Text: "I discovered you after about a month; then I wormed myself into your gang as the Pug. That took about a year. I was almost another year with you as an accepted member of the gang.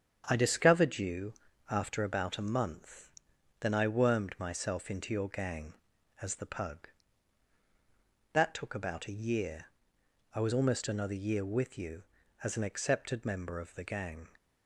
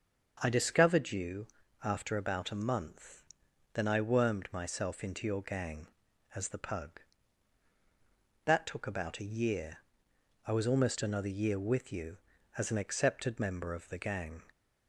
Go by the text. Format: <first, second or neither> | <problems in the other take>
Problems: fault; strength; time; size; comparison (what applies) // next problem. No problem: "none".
second | gets quieter; noticeable; throughout; 5 dB // starts louder than the rest; strong; until 1.2 s; 7.5 dB; also in the second // pauses between "you" and "after"; slight; at 1.3 s; 0.34 s long; slight in the second